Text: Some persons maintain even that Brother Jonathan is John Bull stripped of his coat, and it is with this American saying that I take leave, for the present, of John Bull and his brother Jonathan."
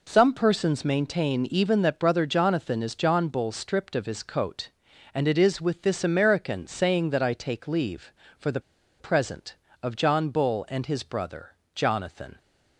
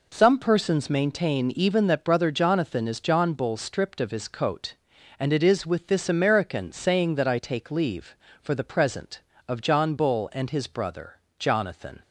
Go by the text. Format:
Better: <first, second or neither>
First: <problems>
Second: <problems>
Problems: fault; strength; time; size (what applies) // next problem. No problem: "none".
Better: second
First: pauses between "the" and "present"; at 8.5 s; 0.40 s long // pauses between "brother" and "Jonathan"; slight; at 11.5 s; 0.24 s long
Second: pauses between "brother" and "Jonathan"; slight; at 11.1 s; 0.24 s long